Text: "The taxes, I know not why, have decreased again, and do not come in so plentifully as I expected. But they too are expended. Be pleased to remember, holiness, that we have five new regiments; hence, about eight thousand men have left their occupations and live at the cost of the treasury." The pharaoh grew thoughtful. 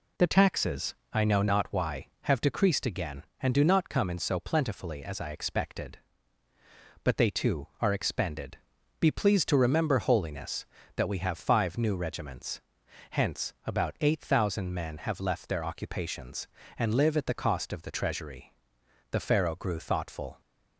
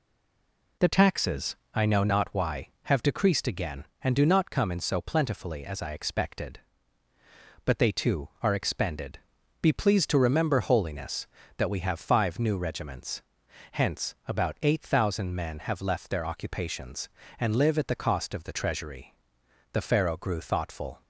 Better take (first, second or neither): first